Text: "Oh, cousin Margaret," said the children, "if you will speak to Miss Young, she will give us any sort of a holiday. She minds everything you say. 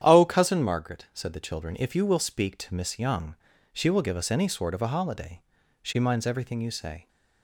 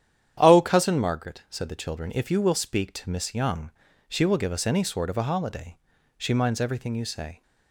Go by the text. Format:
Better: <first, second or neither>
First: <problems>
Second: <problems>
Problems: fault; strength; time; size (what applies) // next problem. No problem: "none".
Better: neither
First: starts louder than the rest; strong; until 1.0 s; 10 dB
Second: starts louder than the rest; strong; until 1.4 s; 10 dB